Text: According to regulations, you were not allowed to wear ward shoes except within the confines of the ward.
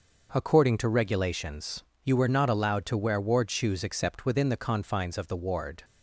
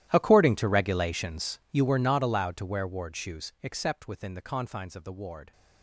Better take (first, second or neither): first